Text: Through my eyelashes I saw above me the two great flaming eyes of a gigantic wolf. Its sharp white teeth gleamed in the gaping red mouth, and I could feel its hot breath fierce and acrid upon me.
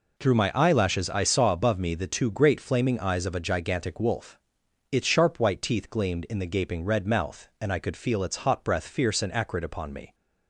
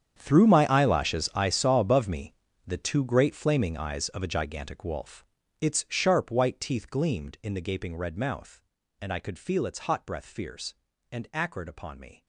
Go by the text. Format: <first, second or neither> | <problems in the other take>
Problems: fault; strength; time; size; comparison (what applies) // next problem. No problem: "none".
first | gets quieter; strong; throughout; 17.5 dB // pauses between "me" and "the"; slight; at 2.3 s; 0.32 s long